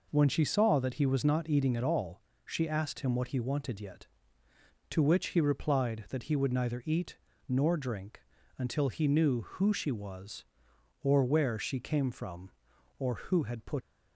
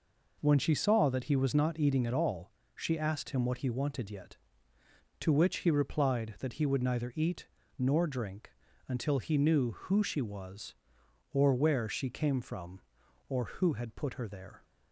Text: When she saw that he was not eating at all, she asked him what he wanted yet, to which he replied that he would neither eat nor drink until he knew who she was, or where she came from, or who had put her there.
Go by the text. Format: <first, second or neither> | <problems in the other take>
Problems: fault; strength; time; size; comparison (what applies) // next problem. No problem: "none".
second | pauses between "eat" and "nor"; slight; at 7.1 s; 0.30 s long; slight in the second // pauses between "drink" and "until"; slight; at 8.2 s; 0.36 s long; slight in the second // stops before "her there"; at 13.8 s